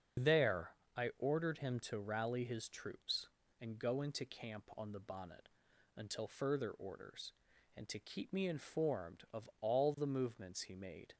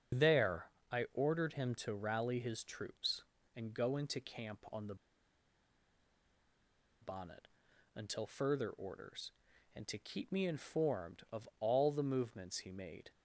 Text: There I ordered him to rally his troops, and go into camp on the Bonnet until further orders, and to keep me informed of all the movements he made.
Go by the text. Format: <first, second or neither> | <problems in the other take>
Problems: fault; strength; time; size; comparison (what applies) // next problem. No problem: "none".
first | starts louder than the rest; until 1.4 s; 7 dB; also in the first // pauses between "There" and "I"; slight; at 0.6 s; 0.24 s long; slight in the first // pauses between "the" and "Bonnet"; strong; at 4.9 s; 2.0 s long // pauses between "Bonnet" and "until"; noticeable; at 7.4 s; 0.48 s long; noticeable in the first